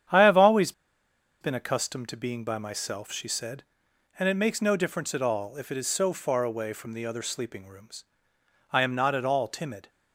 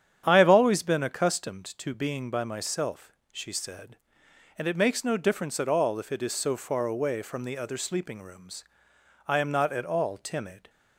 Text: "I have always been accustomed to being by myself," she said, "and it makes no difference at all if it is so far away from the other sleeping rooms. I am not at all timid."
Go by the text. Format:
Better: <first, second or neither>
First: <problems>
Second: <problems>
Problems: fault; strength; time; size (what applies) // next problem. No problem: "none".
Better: second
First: starts louder than the rest; strong; until 1.8 s; 9 dB // pauses between "always" and "been"; noticeable; at 0.7 s; 0.69 s long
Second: starts louder than the rest; strong; until 1.2 s; 9 dB